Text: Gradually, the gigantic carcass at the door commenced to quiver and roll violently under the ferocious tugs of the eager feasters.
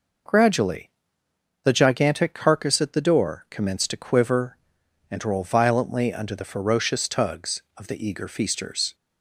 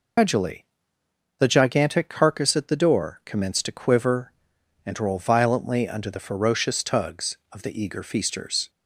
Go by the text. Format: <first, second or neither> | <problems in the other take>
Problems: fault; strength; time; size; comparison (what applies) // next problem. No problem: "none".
first | loses the start of "Gradually"; at 0.1 s; 165 ms